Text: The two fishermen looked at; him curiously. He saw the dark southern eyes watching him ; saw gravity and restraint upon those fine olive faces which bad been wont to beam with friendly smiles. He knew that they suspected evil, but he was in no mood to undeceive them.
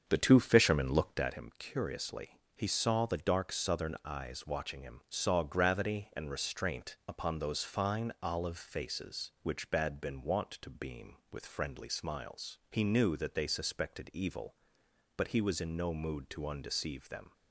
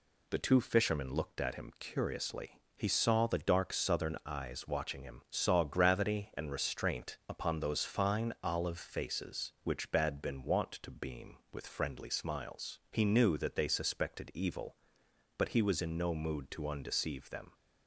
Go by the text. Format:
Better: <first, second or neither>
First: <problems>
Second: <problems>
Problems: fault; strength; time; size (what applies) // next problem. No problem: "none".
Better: second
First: starts louder than the rest; strong; until 1.3 s; 7 dB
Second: none